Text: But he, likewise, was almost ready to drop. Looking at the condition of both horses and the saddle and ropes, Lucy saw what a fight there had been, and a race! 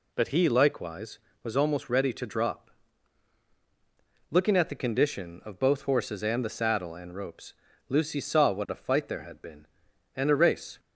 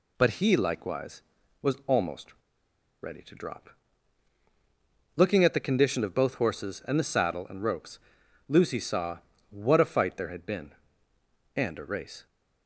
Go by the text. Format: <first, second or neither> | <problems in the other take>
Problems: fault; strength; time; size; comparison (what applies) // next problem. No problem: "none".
first | pauses between "almost" and "ready"; noticeable; at 2.3 s; 0.68 s long // pauses between "saw" and "what"; slight; at 9.1 s; 0.32 s long